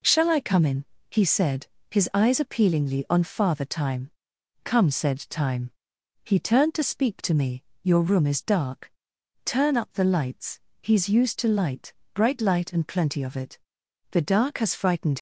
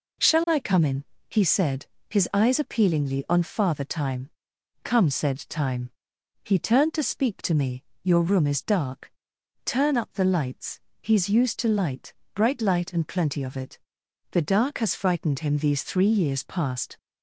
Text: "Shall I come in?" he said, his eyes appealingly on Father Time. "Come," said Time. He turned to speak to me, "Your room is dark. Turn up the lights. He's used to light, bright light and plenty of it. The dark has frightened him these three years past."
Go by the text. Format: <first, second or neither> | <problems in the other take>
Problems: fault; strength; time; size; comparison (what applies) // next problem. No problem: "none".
second | stops before "him these three years past"; at 15.1 s